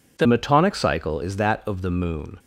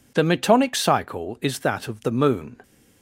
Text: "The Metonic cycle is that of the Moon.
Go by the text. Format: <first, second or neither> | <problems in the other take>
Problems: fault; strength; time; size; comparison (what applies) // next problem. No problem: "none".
second | changes voice at "Metonic"; from 0.2 s on; 2.1 s long